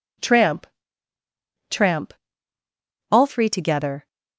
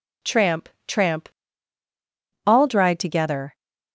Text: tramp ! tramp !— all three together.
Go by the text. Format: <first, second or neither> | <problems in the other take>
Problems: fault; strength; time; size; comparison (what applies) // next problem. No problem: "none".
first | says "dried" for "three"; at 2.6 s